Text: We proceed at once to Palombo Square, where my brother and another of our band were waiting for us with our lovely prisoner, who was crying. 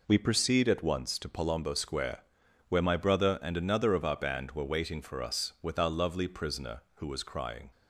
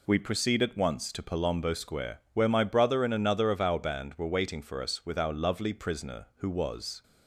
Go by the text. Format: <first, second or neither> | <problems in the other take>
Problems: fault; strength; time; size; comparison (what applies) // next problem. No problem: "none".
first | stops before "crying"; at 7.0 s